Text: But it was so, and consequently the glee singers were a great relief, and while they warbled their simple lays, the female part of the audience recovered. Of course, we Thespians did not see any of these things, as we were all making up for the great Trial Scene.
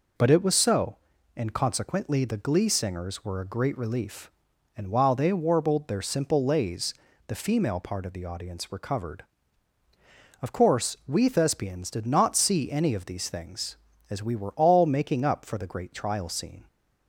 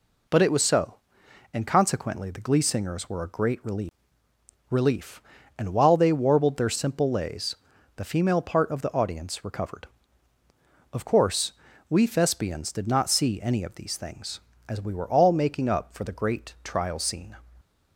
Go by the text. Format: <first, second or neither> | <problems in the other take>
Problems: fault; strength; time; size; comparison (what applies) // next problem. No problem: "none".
first | says "relief" twice; at 4.6 s